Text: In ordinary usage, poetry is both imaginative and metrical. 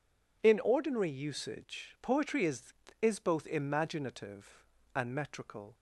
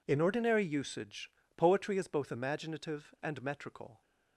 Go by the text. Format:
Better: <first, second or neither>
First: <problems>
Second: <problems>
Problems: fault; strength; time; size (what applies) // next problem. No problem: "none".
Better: second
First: says "is" twice; at 3.0 s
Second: none